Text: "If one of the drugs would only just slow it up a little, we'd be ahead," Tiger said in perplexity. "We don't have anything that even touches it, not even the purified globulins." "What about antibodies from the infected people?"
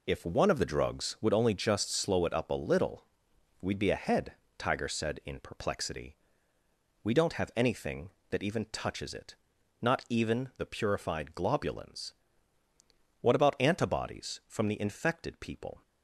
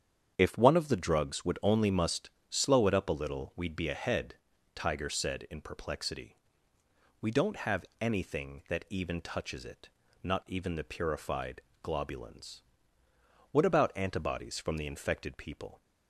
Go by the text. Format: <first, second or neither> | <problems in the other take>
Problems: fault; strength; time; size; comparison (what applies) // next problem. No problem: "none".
first | starts louder than the rest; strong; until 1.3 s; 8 dB // says "must" for "just"; at 1.8 s // pauses between "have" and "anything"; slight; at 7.8 s; 0.16 s long // pauses between "purified" and "globulins"; slight; at 11.6 s; 0.20 s long